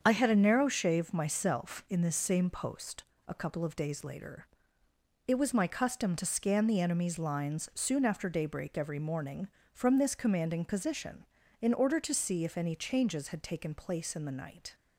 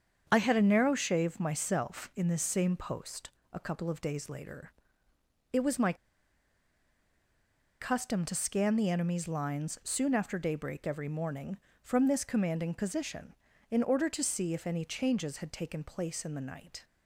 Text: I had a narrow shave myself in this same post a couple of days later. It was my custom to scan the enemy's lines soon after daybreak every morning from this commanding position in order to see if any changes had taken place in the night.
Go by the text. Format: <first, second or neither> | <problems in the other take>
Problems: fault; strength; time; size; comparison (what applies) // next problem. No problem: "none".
first | starts louder than the rest; strong; until 1.3 s; 7 dB; strong in the first // pauses between "post" and "a"; slight; at 3.2 s; 0.20 s long; slight in the first // pauses between "my" and "custom"; strong; at 5.9 s; 1.8 s long